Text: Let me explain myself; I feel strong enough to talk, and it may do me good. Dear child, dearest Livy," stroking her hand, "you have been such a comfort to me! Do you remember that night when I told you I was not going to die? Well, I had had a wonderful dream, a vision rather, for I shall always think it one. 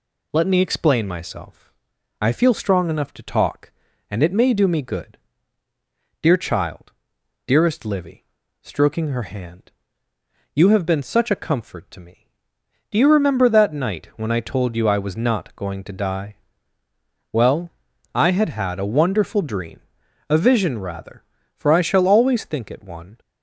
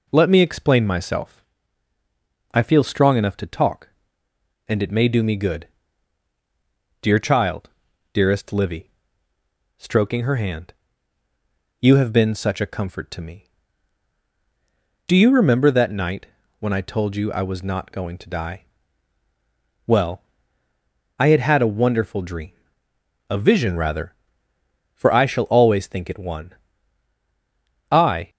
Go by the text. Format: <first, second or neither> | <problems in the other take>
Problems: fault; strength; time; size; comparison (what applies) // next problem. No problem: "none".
first | pauses between "night" and "when"; slight; at 16.2 s; 0.32 s long // goes on to say "I"; slight; from 27.9 s on; 0.38 s long